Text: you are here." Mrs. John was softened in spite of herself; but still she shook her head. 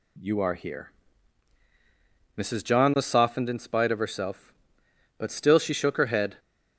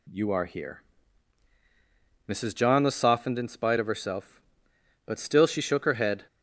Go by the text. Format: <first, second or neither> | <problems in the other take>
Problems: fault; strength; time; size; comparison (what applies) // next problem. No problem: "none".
neither | none